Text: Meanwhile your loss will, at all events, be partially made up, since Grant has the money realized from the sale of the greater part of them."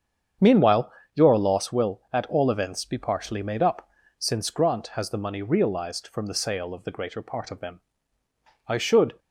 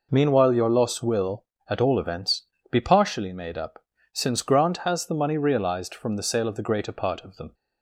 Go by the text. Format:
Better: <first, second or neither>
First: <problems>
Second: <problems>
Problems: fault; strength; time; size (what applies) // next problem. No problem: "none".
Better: second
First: starts louder than the rest; strong; until 1.6 s; 8 dB // pauses between "Meanwhile" and "your"; slight; at 0.9 s; 0.22 s long // goes on to say "I should"; from 8.6 s on; 0.50 s long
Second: none